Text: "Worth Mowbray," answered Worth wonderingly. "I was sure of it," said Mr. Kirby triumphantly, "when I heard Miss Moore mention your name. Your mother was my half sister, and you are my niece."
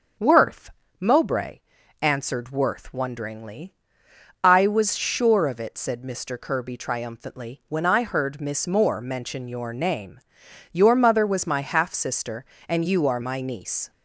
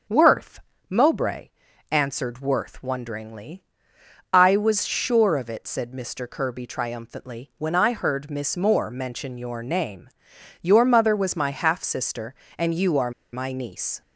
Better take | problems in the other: first | starts louder than the rest; until 1.3 s; 6.5 dB; also in the first // pauses between "Worth" and "Mowbray"; slight; at 0.6 s; 0.26 s long; slight in the first // pauses between "are" and "my"; slight; at 13.1 s; 0.21 s long

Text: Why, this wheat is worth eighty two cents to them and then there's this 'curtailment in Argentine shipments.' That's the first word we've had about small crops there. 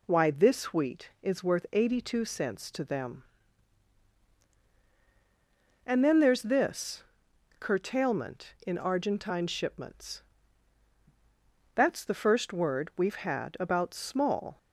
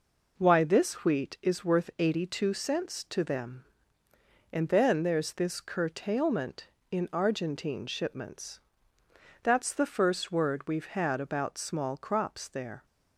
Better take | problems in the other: second | pauses between "this" and "curtailment"; noticeable; at 7.0 s; 0.56 s long // stops before "crops there"; at 14.5 s

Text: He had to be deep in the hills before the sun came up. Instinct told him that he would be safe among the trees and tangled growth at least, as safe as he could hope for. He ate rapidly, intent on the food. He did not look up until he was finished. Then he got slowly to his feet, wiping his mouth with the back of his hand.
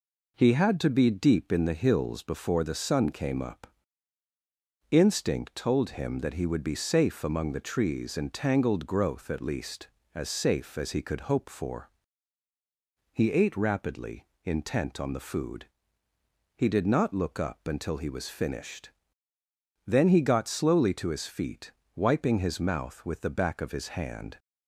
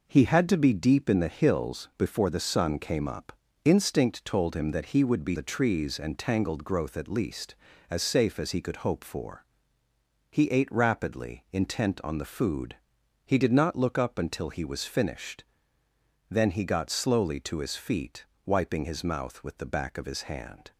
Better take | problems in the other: first | skips "safe among"; at 5.3 s

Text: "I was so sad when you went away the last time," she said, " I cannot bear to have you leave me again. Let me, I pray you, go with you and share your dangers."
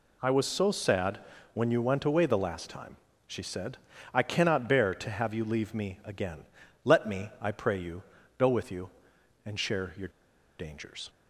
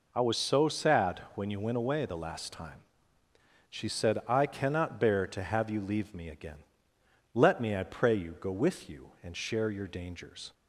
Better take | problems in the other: second | pauses between "sad" and "when"; slight; at 1.1 s; 0.34 s long; slight in the second // pauses between "your" and "dangers"; noticeable; at 10.0 s; 0.49 s long

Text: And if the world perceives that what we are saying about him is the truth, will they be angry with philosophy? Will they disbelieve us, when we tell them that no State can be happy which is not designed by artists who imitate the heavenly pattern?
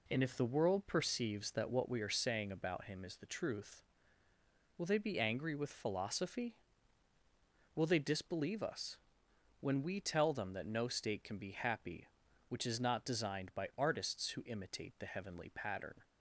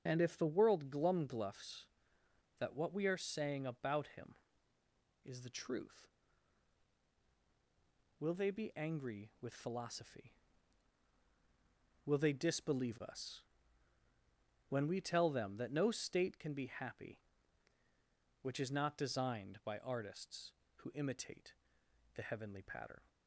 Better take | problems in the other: first | starts louder than the rest; strong; until 1.0 s; 7.5 dB // says "glumgluffs" for "perceives"; at 0.8 s // pauses between "imitate" and "the"; noticeable; at 21.5 s; 0.62 s long

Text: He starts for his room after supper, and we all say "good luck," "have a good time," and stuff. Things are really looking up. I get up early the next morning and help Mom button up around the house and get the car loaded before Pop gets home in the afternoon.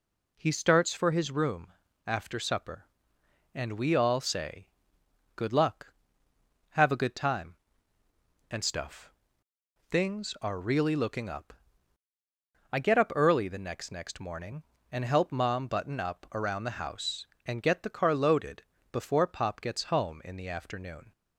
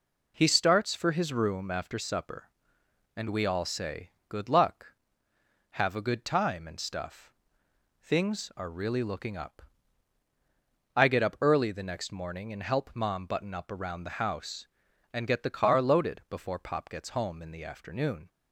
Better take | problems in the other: second | pauses between "room" and "after"; slight; at 1.7 s; 0.34 s long // pauses between "say" and "good"; noticeable; at 4.6 s; 0.70 s long; slight in the second // says "next" twice; at 13.9 s // pauses between "loaded" and "before"; slight; at 18.6 s; 0.28 s long

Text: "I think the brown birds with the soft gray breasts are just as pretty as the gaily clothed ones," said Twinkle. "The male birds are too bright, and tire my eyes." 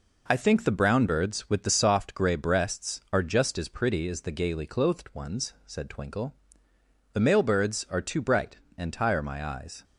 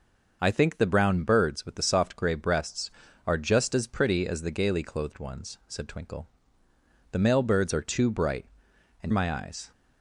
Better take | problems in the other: first | starts louder than the rest; noticeable; until 1.4 s; 6 dB // skips "tire"; at 9.1 s

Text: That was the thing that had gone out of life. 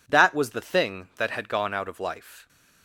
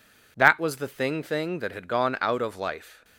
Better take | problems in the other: first | says "thing" twice; at 1.2 s

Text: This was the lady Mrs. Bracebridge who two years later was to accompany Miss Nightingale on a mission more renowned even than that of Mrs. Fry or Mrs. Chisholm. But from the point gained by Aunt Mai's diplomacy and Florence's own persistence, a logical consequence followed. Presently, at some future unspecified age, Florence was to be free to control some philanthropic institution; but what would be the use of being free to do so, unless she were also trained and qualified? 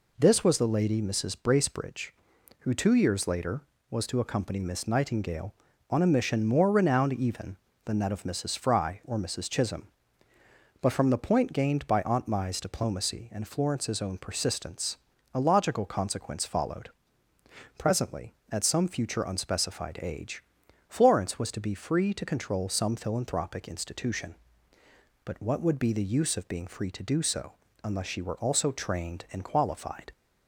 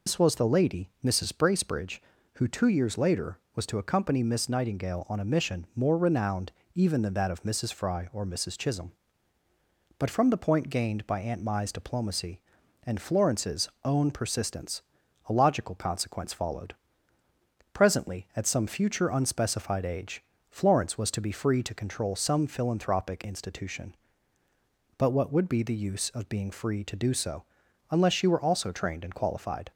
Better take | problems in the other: first | loses the start of "This"; at 0.0 s; 105 ms // pauses between "renowned" and "even"; slight; at 6.5 s; 0.24 s long // pauses between "Florence's" and "own"; slight; at 13.6 s; 0.16 s long

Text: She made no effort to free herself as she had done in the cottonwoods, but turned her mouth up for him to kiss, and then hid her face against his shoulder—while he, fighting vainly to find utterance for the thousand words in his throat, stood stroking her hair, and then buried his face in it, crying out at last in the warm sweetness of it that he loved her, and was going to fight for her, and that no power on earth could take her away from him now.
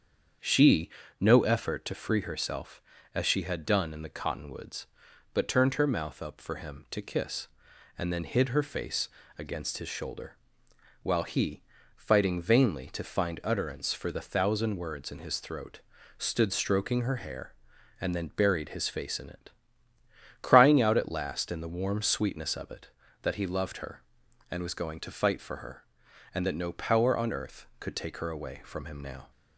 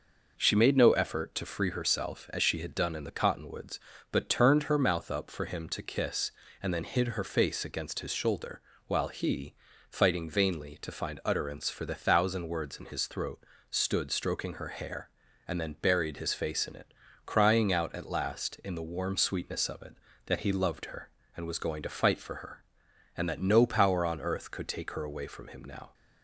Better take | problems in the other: second | starts louder than the rest; strong; until 1.7 s; 7.5 dB // skips "made"; at 1.0 s // pauses between "face" and "against"; slight; at 9.0 s; 0.28 s long

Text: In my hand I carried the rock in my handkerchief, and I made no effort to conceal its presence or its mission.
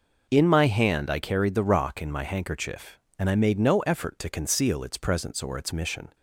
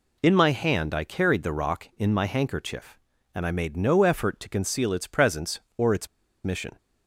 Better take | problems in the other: first | pauses between "its" and "mission"; at 6.0 s; 0.36 s long

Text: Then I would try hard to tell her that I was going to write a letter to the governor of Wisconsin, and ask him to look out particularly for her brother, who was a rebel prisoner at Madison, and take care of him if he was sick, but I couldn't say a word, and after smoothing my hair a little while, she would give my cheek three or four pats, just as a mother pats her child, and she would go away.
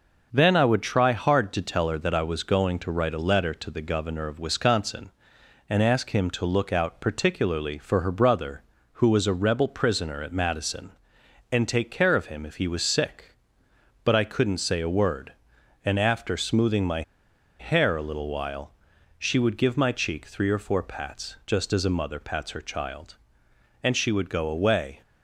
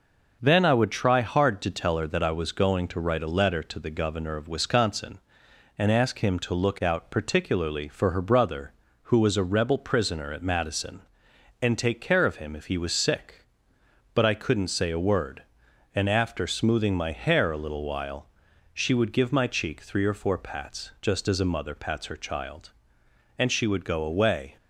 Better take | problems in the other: second | starts louder than the rest; noticeable; until 1.3 s; 6 dB // pauses between "my" and "hair"; noticeable; at 17.0 s; 0.57 s long

